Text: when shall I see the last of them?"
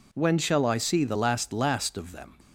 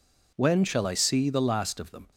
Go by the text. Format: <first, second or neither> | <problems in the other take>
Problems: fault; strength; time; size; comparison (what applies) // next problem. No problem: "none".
second | says "last" twice; at 1.5 s